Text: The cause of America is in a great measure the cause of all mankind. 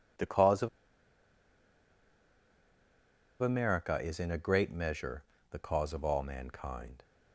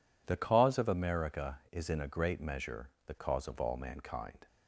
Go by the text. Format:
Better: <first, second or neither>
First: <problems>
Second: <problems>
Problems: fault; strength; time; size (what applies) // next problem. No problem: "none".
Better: second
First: pauses between "of" and "America"; strong; at 0.6 s; 2.7 s long // pauses between "measure" and "the"; slight; at 5.2 s; 0.26 s long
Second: pauses between "measure" and "the"; slight; at 2.8 s; 0.16 s long